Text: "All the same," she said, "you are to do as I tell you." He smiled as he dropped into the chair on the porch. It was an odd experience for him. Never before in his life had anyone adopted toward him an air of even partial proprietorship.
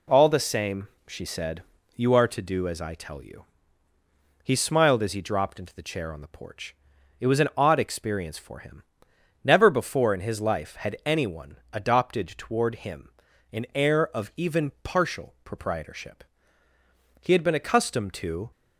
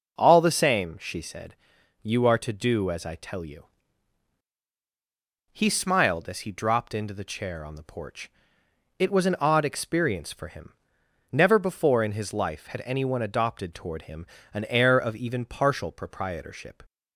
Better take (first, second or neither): second